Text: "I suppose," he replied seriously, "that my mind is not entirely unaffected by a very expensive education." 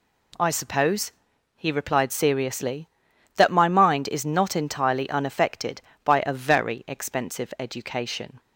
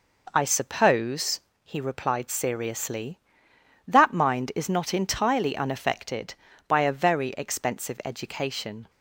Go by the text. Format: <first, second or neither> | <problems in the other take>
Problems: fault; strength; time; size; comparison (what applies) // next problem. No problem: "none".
first | skips "my"; at 4.1 s